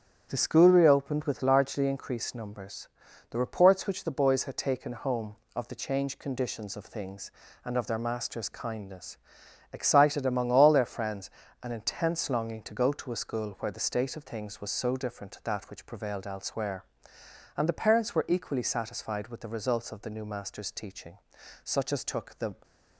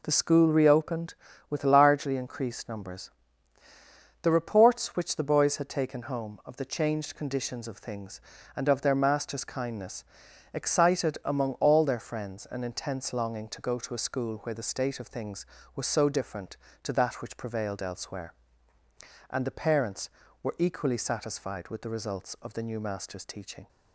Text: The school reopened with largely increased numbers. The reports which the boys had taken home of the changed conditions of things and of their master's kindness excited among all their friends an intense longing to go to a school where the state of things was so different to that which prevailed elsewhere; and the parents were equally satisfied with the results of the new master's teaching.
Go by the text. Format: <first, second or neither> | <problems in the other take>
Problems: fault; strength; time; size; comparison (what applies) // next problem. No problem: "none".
second | starts louder than the rest; strong; until 1.3 s; 9 dB // pauses between "kindness" and "excited"; noticeable; at 9.1 s; 0.54 s long; noticeable in the second // pauses between "friends" and "an"; slight; at 11.2 s; 0.34 s long // goes on to say "Such as took the"; noticeable; from 21.6 s on; 0.90 s long